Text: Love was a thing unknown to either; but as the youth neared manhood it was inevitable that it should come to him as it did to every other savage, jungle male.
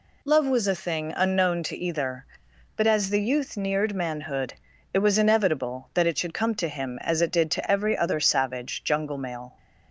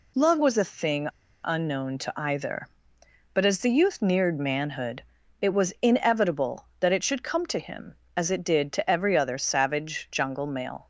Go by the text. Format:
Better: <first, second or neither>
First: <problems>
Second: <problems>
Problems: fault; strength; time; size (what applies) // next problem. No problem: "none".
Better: first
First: pauses between "manhood" and "it"; at 4.5 s; 0.40 s long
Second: pauses between "thing" and "unknown"; slight; at 1.0 s; 0.34 s long // pauses between "manhood" and "it"; at 5.0 s; 0.40 s long